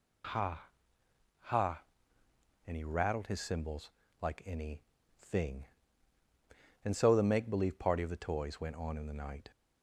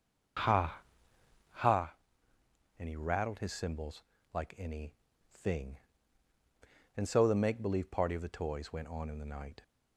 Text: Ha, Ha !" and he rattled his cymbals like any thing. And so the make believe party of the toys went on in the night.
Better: first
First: pauses between "cymbals" and "like"; slight; at 3.9 s; 0.28 s long // pauses between "any" and "thing"; slight; at 4.8 s; 0.36 s long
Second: starts louder than the rest; until 1.8 s; 6.5 dB // pauses between "cymbals" and "like"; slight; at 4.0 s; 0.28 s long // pauses between "any" and "thing"; slight; at 4.9 s; 0.36 s long

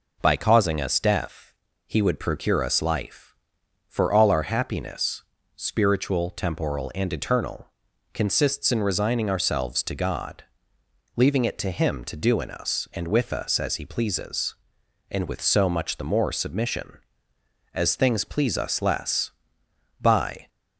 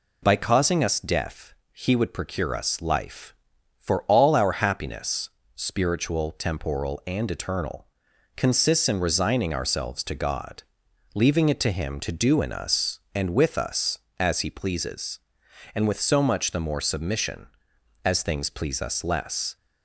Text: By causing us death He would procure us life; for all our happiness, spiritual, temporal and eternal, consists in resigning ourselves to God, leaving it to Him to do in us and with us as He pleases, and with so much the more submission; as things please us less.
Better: second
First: pauses between "death" and "He"; slight; at 1.5 s; 0.34 s long // goes on to say "By"; slight; from 20.0 s on; 0.46 s long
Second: pauses between "death" and "He"; slight; at 1.5 s; 0.20 s long

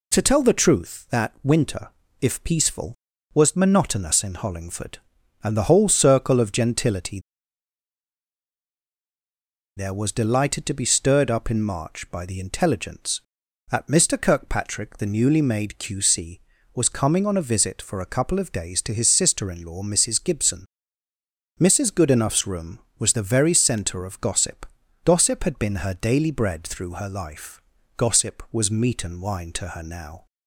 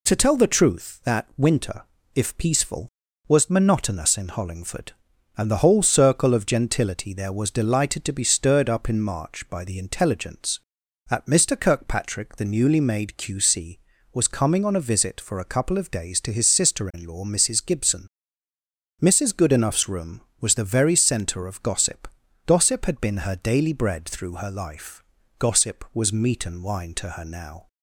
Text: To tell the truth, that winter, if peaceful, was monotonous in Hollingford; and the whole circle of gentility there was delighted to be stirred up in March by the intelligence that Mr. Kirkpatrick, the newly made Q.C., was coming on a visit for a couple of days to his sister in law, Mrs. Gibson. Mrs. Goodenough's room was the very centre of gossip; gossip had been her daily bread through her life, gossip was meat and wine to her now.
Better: second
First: pauses between "gentility" and "there"; strong; at 7.1 s; 2.5 s long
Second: none

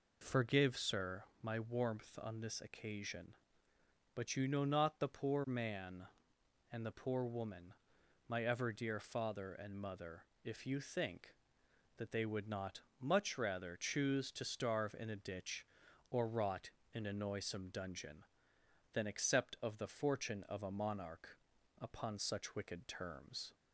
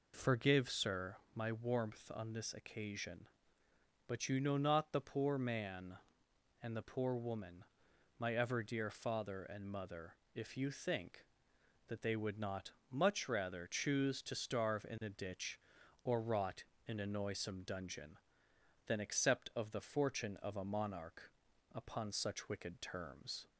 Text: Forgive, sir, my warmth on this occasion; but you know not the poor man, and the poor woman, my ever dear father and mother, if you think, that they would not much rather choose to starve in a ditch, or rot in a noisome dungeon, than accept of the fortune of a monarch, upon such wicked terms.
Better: neither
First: pauses between "not" and "much"; slight; at 12.8 s; 0.20 s long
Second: pauses between "not" and "much"; slight; at 12.7 s; 0.20 s long

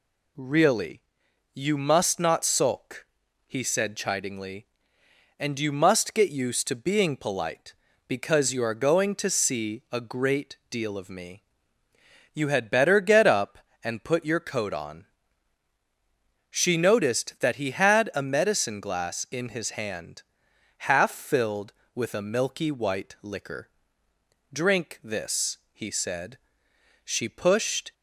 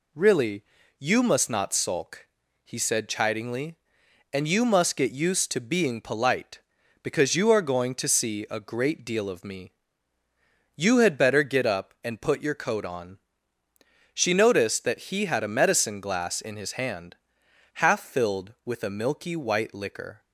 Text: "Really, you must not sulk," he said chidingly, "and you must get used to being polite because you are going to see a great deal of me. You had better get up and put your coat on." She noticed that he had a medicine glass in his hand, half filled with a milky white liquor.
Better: second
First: goes on to say "Drink this he said She pushed"; strong; from 24.5 s on; 3.4 s long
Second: none

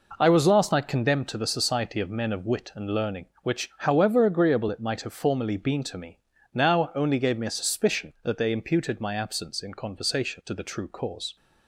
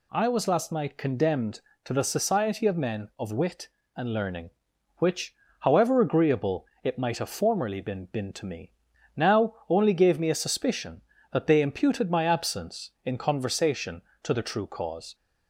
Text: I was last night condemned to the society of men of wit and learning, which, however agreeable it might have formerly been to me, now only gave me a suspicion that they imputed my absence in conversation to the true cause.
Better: first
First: none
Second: pauses between "agreeable" and "it"; slight; at 6.6 s; 0.18 s long // says "been" twice; at 8.0 s

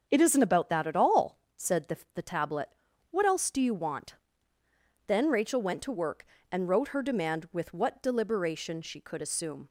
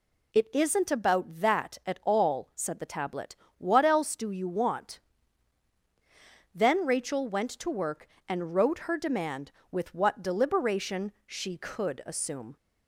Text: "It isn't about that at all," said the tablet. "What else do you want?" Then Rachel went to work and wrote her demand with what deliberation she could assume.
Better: second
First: starts louder than the rest; until 1.1 s; 7 dB // says "the" twice; at 2.1 s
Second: none

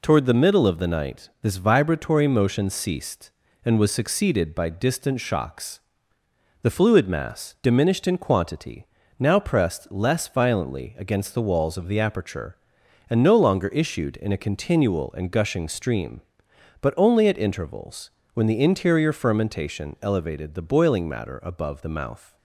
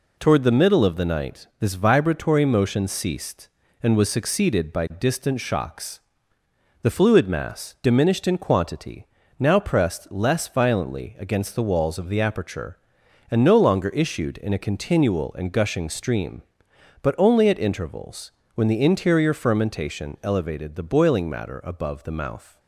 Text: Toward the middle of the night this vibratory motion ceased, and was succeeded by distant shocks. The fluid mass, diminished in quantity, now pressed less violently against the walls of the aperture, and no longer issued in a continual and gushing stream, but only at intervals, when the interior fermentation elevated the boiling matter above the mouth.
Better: neither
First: none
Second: none

